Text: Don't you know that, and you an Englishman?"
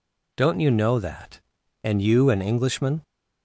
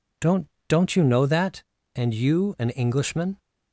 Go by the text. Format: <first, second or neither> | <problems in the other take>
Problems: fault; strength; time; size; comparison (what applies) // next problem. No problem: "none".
first | says "Don't" twice; at 0.6 s